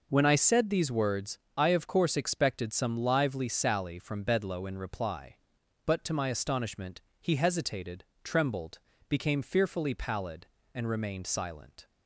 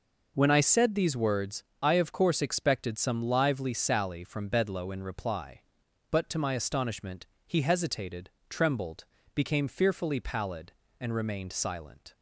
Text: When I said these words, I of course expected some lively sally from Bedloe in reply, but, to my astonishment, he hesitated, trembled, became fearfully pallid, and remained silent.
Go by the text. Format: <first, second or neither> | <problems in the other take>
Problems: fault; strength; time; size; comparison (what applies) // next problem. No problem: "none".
neither | none